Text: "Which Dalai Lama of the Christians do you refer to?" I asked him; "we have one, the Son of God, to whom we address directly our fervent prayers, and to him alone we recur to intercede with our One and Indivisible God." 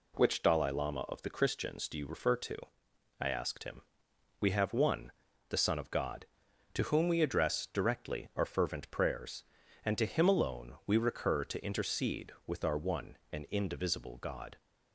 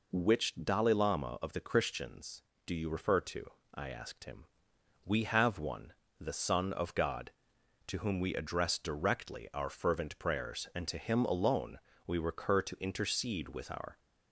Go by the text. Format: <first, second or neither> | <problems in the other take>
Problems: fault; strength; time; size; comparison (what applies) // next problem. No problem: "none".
first | pauses between "alone" and "we"; slight; at 11.7 s; 0.28 s long // stops before "One and Indivisible God"; at 13.9 s